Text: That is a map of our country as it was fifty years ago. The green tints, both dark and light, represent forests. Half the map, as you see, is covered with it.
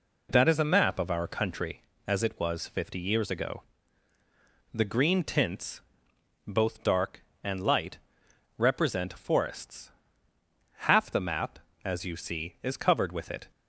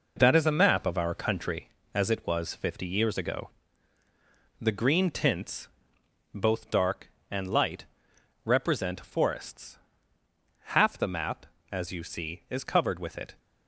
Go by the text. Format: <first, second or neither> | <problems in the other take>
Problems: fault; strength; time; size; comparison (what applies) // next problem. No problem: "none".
first | gets quieter; throughout; 7 dB